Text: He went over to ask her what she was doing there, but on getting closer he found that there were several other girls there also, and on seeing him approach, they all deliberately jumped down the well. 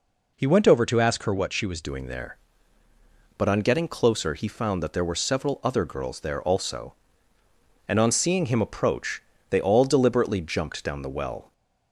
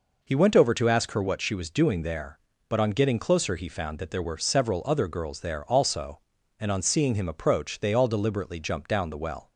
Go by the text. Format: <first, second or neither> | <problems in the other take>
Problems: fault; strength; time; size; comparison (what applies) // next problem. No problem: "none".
second | changes voice at "doing"; from 1.8 s on; 9.7 s long